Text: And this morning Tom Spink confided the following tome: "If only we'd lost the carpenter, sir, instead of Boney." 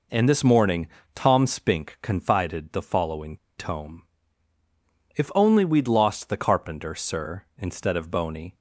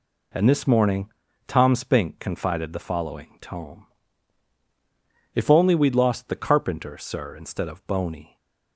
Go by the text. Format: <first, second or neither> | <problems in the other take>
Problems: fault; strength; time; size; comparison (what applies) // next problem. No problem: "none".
second | pauses between "morning" and "Tom"; slight; at 0.8 s; 0.28 s long; also in the second // pauses between "following" and "tome"; slight; at 3.3 s; 0.21 s long